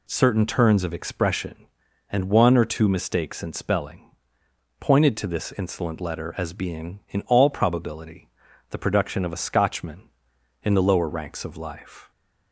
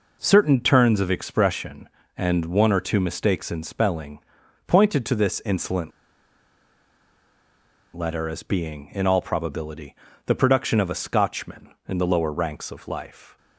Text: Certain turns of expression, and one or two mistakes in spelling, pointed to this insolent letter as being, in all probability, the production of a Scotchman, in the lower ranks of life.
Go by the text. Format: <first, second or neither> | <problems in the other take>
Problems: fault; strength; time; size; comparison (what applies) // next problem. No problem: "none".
first | pauses between "insolent" and "letter"; strong; at 5.9 s; 2.0 s long